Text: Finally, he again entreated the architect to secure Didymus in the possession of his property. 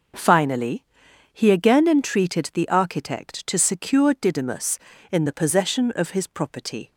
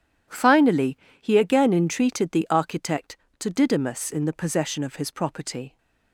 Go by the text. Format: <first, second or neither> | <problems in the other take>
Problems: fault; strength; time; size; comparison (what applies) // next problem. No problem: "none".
first | skips "secure"; at 3.4 s